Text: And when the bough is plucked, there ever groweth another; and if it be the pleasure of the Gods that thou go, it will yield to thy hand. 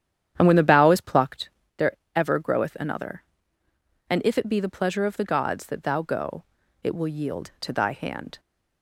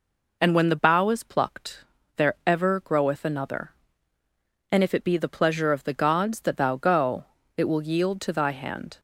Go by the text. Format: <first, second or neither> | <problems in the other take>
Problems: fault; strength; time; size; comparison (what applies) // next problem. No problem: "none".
second | starts louder than the rest; strong; until 1.8 s; 9.5 dB // pauses between "there" and "ever"; slight; at 1.9 s; 0.18 s long